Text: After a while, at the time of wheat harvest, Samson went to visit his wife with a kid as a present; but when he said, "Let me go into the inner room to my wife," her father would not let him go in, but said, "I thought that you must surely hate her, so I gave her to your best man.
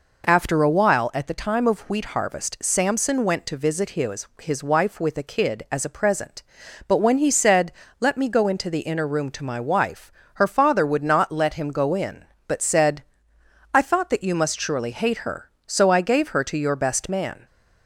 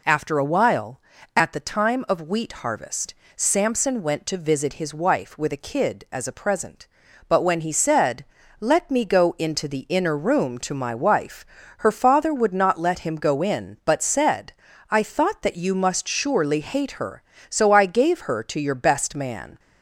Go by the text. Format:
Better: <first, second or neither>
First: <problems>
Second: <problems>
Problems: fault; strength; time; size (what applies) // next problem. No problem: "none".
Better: second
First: says "his" twice; at 4.4 s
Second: none